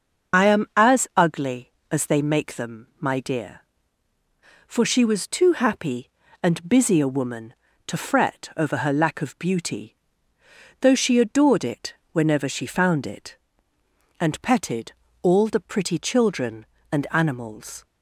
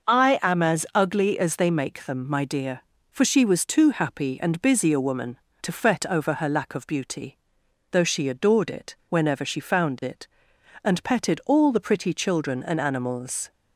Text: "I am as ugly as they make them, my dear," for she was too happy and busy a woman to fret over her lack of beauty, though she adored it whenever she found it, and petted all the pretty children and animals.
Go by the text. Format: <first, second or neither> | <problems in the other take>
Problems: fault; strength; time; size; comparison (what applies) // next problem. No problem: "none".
second | loses the start of "I"; at 0.3 s; 60 ms // starts louder than the rest; until 1.5 s; 6.5 dB // pauses between "it" and "whenever"; slight; at 11.9 s; 0.18 s long // pauses between "petted" and "all"; slight; at 14.9 s; 0.30 s long